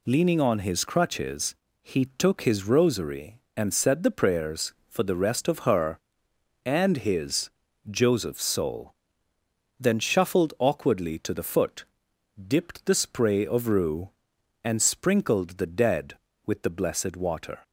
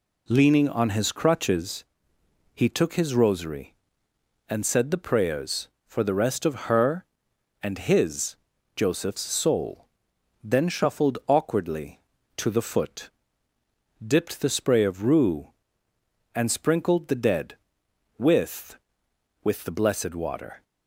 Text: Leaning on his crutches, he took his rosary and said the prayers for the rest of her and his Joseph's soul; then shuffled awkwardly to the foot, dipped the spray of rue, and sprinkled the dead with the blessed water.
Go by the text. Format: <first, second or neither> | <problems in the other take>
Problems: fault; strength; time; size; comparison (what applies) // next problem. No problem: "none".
first | pauses between "his" and "Joseph's"; at 8.3 s; 0.40 s long; also in the first // says "with" twice; at 19.4 s